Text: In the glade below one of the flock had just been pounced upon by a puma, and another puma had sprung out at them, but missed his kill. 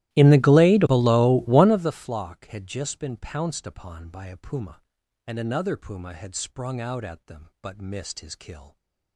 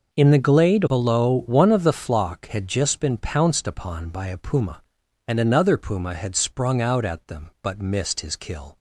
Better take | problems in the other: second | starts louder than the rest; strong; until 1.9 s; 15.5 dB

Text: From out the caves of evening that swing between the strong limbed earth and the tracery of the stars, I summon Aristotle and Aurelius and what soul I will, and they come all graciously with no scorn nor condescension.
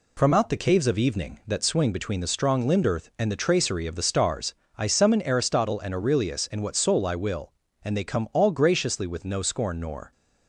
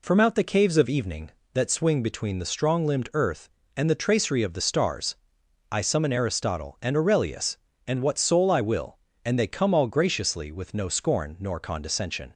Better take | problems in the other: second | stops before "condescension"; at 10.1 s

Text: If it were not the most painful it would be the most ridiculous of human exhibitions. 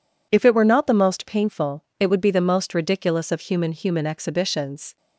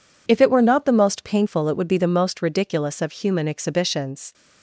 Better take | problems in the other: second | pauses between "painful" and "it"; slight; at 1.8 s; 0.18 s long // says "human" twice; at 3.7 s

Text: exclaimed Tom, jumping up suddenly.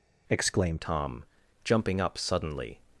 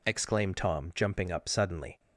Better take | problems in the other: second | changes voice at "Tom"; from 0.8 s on; 2.0 s long

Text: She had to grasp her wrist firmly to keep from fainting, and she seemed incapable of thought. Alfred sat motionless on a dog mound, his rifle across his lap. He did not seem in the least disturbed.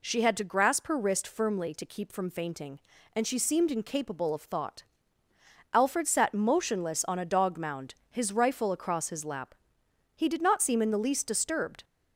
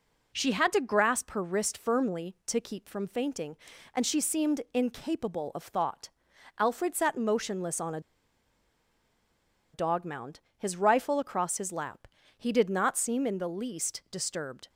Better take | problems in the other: first | pauses between "a" and "dog"; strong; at 7.9 s; 1.7 s long

